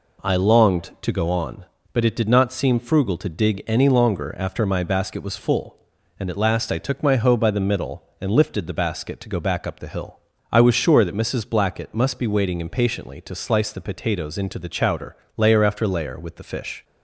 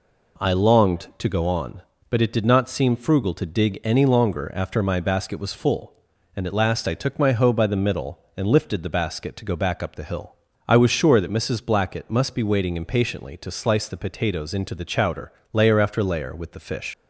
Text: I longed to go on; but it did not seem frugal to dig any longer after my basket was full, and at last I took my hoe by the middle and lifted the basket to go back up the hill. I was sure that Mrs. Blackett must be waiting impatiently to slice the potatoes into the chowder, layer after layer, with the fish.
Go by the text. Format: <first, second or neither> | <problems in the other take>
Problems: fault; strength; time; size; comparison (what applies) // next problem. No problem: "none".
first | leaves "fish" unfinished; at 16.9 s; 80 ms